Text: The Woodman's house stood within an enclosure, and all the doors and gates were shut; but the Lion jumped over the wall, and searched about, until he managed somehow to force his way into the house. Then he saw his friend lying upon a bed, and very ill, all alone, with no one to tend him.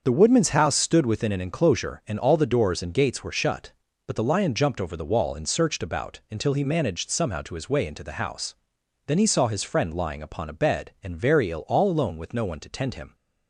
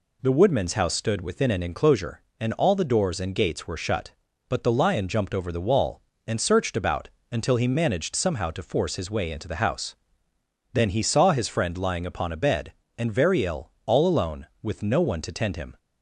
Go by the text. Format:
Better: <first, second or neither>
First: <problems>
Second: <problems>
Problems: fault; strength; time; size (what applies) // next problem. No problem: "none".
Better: second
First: starts louder than the rest; until 1.0 s; 6.5 dB // skips "force"; at 7.5 s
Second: none